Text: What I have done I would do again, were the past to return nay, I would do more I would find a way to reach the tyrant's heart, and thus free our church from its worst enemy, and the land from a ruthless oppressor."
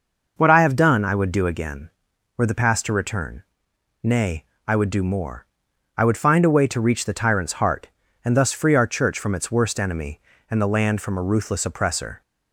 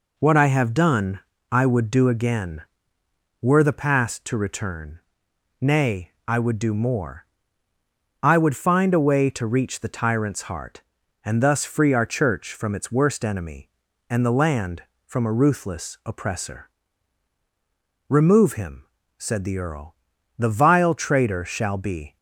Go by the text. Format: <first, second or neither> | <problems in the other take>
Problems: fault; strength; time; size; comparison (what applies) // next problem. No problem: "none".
first | pauses between "done" and "I"; slight; at 1.1 s; 0.32 s long // pauses between "return" and "nay"; noticeable; at 4.9 s; 0.62 s long; noticeable in the first // pauses between "more" and "I"; noticeable; at 7.2 s; 0.96 s long; noticeable in the first // goes on to say "Remove him said the earl the vile traitor shall be"; strong; from 18.0 s on; 4.0 s long